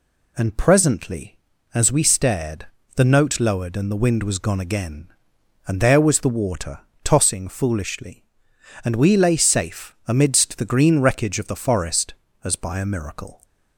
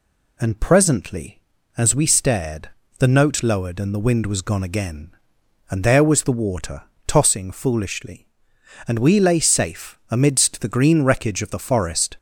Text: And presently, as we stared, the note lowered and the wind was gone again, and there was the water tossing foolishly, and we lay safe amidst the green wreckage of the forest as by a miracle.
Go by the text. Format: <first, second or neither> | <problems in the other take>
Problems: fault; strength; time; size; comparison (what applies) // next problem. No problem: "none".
first | pauses between "water" and "tossing"; slight; at 6.8 s; 0.24 s long; slight in the first // stops before "as by a miracle"; at 12.1 s